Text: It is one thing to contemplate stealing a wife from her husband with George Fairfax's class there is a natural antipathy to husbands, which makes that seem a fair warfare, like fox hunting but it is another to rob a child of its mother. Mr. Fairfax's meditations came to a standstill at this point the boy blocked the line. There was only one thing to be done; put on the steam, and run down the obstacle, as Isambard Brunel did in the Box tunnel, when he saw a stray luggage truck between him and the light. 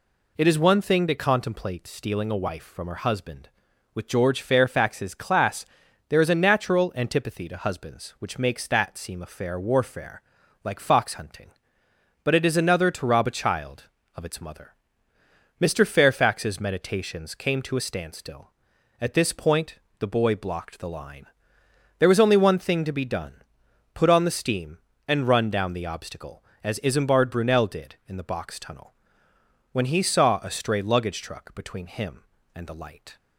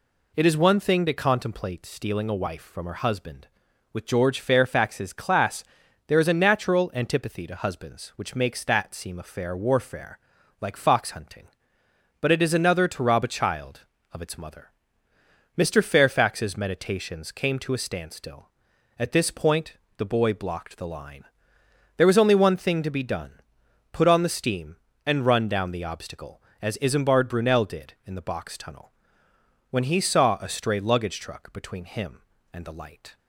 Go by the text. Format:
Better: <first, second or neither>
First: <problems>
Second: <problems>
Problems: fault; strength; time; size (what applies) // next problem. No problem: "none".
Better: neither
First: pauses between "class" and "there"; at 5.6 s; 0.44 s long // pauses between "point" and "the"; slight; at 19.7 s; 0.22 s long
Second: pauses between "class" and "there"; at 5.6 s; 0.44 s long // pauses between "point" and "the"; slight; at 19.7 s; 0.22 s long